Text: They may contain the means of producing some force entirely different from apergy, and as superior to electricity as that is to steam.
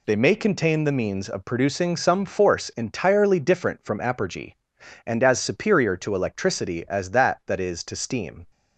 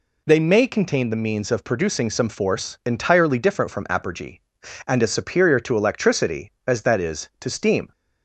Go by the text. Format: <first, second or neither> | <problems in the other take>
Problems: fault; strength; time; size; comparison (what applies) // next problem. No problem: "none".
second | says "that" twice; at 7.4 s